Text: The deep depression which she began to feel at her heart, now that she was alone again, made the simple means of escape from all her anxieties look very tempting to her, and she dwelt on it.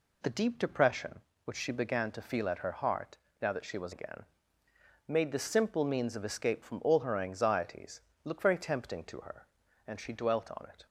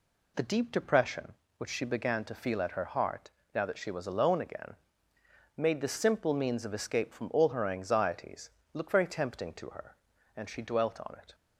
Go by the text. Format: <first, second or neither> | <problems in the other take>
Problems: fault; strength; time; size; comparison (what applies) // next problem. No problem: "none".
second | skips "alone"; at 3.9 s // pauses between "anxieties" and "look"; slight; at 7.9 s; 0.24 s long; slight in the second